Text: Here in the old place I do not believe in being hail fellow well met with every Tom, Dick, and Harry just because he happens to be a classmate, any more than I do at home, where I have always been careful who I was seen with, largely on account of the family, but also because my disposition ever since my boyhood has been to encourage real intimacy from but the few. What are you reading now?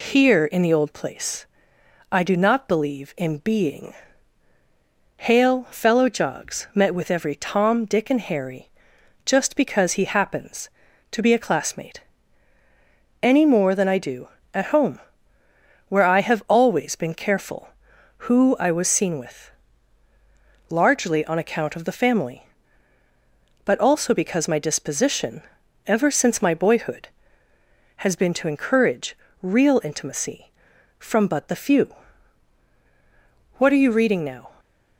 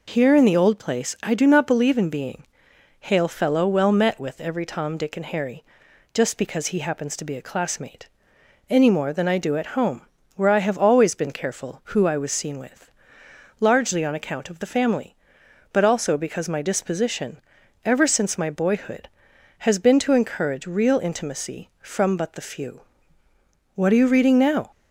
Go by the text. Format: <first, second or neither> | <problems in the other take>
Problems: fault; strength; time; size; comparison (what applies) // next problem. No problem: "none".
second | pauses between "place" and "I"; noticeable; at 1.4 s; 0.66 s long // pauses between "being" and "hail"; at 3.9 s; 1.2 s long; noticeable in the second // says "jogs" for "well"; at 6.0 s // pauses between "Harry" and "just"; noticeable; at 8.6 s; 0.58 s long; noticeable in the second // pauses between "disposition" and "ever"; noticeable; at 25.4 s; 0.46 s long; noticeable in the second // pauses between "encourage" and "real"; slight; at 29.1 s; 0.28 s long